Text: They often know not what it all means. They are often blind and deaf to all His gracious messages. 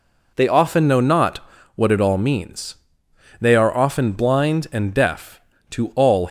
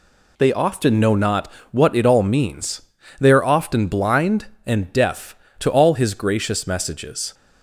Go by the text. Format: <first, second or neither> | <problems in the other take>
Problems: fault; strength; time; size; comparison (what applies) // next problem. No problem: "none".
second | pauses between "not" and "what"; slight; at 1.3 s; 0.36 s long; slight in the second // stops before "His gracious messages"; at 6.2 s